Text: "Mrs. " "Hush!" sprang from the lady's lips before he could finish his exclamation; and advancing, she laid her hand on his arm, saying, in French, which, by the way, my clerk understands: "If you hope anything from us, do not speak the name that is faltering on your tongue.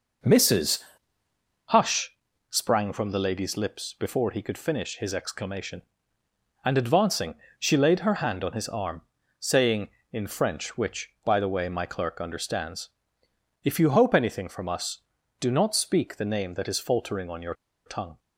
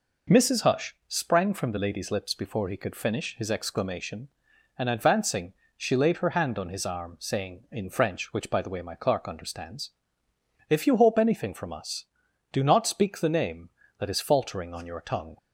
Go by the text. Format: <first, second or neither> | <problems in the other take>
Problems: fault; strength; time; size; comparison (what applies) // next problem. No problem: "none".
second | pauses between "your" and "tongue"; slight; at 17.5 s; 0.31 s long